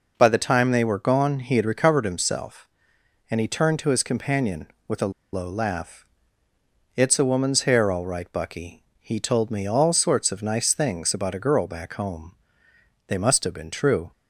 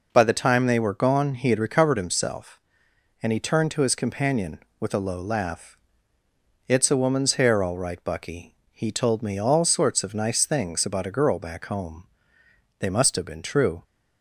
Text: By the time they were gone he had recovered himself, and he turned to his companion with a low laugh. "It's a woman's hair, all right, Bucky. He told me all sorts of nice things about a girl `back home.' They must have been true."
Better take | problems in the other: second | pauses between "a" and "low"; slight; at 5.1 s; 0.20 s long

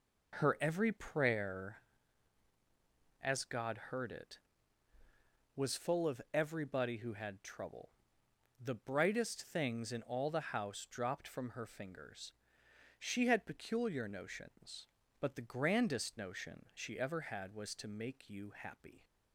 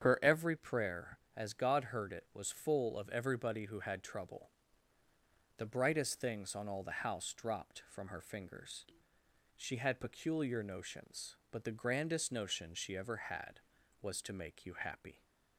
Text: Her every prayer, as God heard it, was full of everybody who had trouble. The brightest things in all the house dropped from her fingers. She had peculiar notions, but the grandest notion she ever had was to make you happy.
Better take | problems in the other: first | starts louder than the rest; strong; until 1.0 s; 8 dB // says "on" for "in"; at 6.5 s

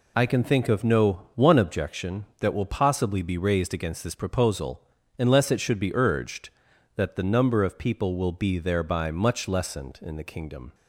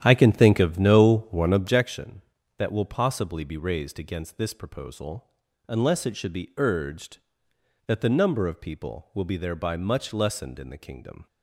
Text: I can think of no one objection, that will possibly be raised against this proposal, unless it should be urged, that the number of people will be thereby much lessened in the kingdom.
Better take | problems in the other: first | starts louder than the rest; strong; until 1.8 s; 10.5 dB

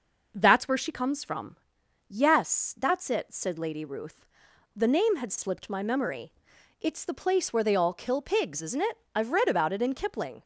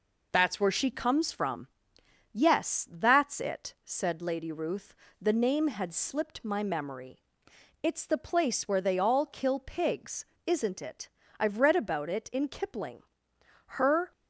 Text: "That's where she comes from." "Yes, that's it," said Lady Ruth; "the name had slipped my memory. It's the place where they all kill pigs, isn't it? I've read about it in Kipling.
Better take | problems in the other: first | goes on to say "Her"; slight; from 13.6 s on; 0.46 s long

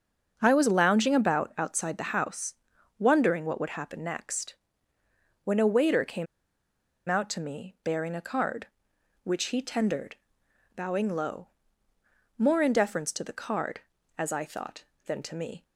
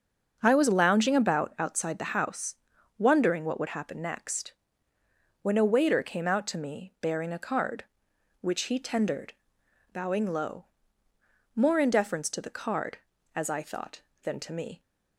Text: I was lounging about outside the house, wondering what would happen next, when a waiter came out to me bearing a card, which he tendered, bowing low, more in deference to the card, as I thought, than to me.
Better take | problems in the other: second | starts louder than the rest; until 1.3 s; 6.5 dB; also in the second // pauses between "came" and "out"; noticeable; at 6.2 s; 0.83 s long

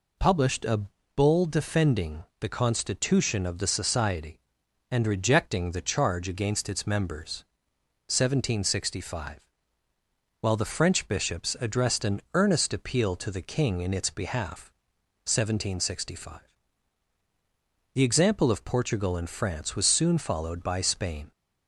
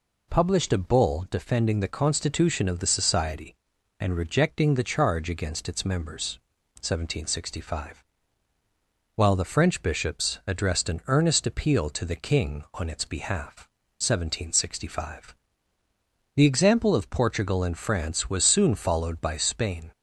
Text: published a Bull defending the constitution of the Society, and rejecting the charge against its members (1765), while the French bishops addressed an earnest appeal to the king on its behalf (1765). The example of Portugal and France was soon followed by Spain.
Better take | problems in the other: second | pauses between "a" and "Bull"; slight; at 0.8 s; 0.34 s long // pauses between "defending" and "the"; slight; at 2.2 s; 0.16 s long // says "in" for "on"; at 13.8 s

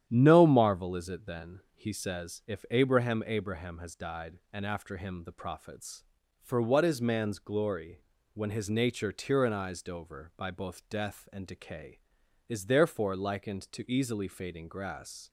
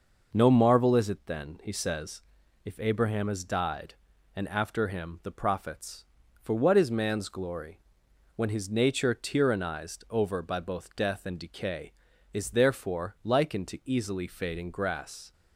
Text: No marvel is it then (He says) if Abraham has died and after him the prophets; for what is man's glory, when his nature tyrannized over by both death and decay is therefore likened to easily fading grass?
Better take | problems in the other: second | starts louder than the rest; strong; until 1.0 s; 10 dB // says "Abraham" twice; at 3.2 s

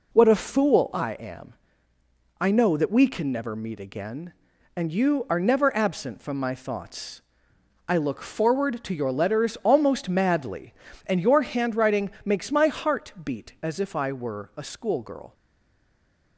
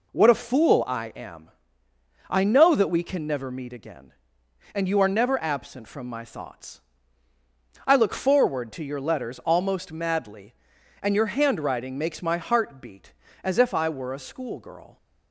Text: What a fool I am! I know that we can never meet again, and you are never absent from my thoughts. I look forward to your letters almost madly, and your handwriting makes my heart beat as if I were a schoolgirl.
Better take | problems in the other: second | pauses between "handwriting" and "makes"; slight; at 12.0 s; 0.16 s long // stays silent after the last word; from 15.3 s on; 1.0 s long

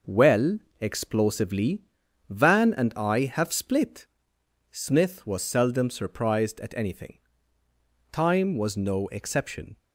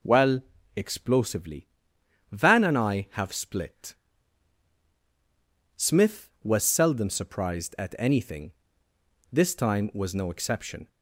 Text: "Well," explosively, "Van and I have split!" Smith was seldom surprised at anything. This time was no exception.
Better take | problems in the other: second | skips "This"; at 7.6 s

